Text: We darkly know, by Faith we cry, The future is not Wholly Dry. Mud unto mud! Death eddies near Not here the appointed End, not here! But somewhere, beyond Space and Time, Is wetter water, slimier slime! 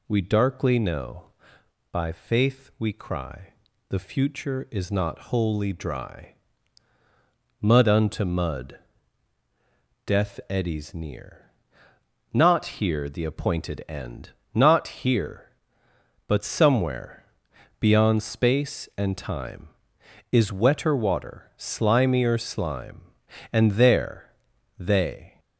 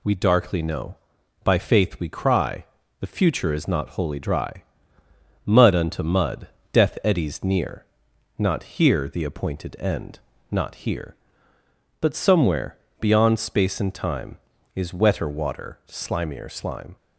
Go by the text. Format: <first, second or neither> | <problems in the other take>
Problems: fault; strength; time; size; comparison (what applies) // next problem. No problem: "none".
second | pauses between "near" and "Not"; noticeable; at 11.4 s; 0.86 s long; noticeable in the second // goes on to say "And there they"; strong; from 23.5 s on; 1.8 s long